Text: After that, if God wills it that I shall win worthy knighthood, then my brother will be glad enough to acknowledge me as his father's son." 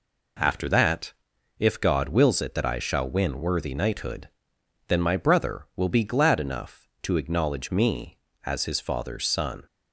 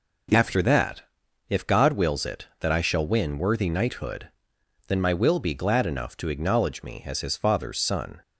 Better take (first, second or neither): first